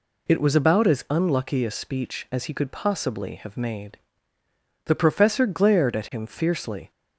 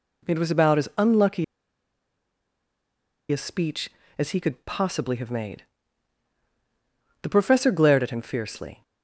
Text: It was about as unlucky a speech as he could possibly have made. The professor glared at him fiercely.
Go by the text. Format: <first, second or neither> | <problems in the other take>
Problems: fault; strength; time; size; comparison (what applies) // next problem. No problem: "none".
first | pauses between "unlucky" and "a"; strong; at 1.4 s; 1.8 s long